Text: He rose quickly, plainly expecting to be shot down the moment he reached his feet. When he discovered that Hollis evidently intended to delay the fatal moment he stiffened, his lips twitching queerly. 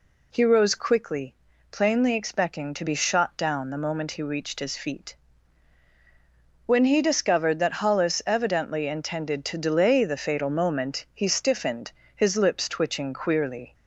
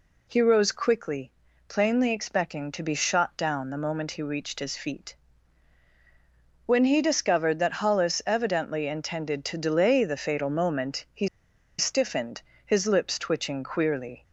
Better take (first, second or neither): first